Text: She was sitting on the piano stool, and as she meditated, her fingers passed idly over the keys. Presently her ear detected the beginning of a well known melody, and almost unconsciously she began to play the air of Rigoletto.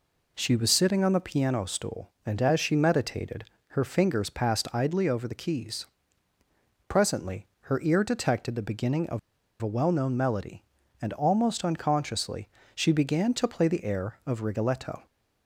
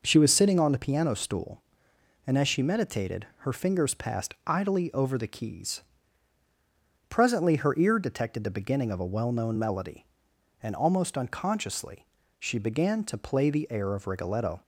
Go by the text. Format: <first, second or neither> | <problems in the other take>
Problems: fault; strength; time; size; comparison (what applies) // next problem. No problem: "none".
second | pauses between "of" and "a"; at 9.1 s; 0.41 s long // pauses between "unconsciously" and "she"; slight; at 12.4 s; 0.26 s long; slight in the second